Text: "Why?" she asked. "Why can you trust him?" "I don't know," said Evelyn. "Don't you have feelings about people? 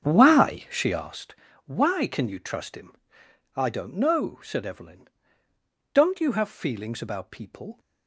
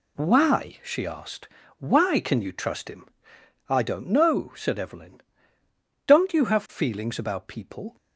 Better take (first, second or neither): second